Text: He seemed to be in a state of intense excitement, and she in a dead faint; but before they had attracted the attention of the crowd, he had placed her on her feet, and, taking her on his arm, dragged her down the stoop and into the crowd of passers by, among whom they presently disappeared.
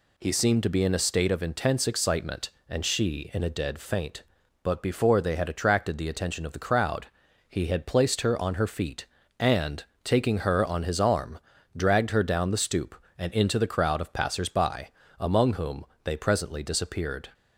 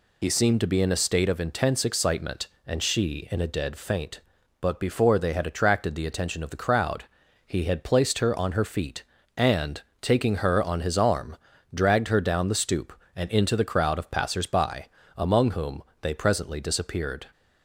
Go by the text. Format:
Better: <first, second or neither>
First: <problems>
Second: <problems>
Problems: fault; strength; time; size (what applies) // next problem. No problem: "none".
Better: first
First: pauses between "whom" and "they"; slight; at 15.8 s; 0.20 s long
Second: loses the start of "He"; at 0.2 s; 60 ms // pauses between "whom" and "they"; slight; at 15.8 s; 0.20 s long